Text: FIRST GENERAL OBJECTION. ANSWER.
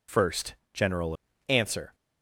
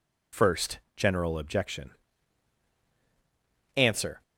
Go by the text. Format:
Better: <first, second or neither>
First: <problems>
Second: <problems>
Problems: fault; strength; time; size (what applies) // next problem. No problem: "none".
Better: second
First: pauses between "FIRST" and "GENERAL"; slight; at 0.5 s; 0.18 s long // skips "OBJECTION"; at 1.3 s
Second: pauses between "FIRST" and "GENERAL"; slight; at 0.7 s; 0.16 s long